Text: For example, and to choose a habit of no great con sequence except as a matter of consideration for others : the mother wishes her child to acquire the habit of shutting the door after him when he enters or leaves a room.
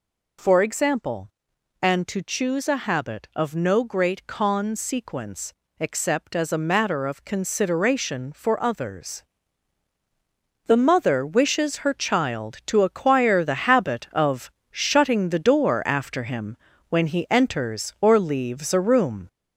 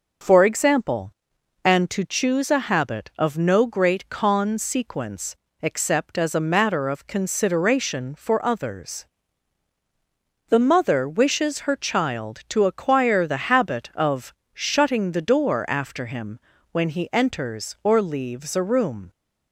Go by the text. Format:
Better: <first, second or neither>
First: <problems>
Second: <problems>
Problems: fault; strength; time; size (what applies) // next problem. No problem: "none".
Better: second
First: gets louder; noticeable; throughout; 5 dB // pauses between "sequence" and "except"; slight; at 5.5 s; 0.26 s long // pauses between "of" and "shutting"; slight; at 14.4 s; 0.22 s long // pauses between "him" and "when"; slight; at 16.5 s; 0.32 s long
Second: pauses between "sequence" and "except"; slight; at 5.3 s; 0.26 s long // pauses between "of" and "shutting"; slight; at 14.3 s; 0.22 s long // pauses between "him" and "when"; slight; at 16.3 s; 0.32 s long